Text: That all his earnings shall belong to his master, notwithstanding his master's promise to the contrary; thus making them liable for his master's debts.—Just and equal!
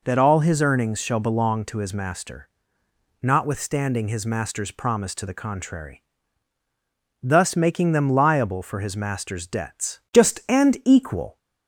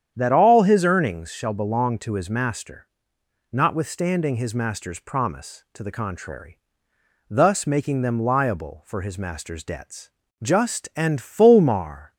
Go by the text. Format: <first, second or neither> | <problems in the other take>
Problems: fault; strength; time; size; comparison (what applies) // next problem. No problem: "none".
first | starts louder than the rest; strong; until 1.1 s; 9 dB // says "fulmar" for "equal"; at 11.1 s